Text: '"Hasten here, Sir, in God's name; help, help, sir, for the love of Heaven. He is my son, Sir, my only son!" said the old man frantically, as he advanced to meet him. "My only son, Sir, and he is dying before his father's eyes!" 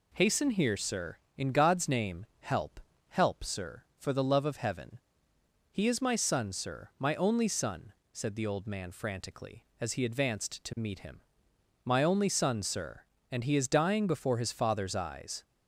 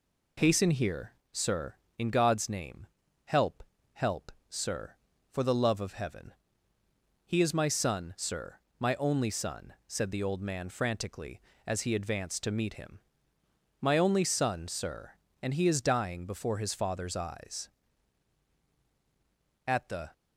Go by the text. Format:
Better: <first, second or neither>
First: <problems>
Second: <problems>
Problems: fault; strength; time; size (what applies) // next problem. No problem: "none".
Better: first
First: none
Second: goes on to say "At the"; slight; from 19.6 s on; 0.46 s long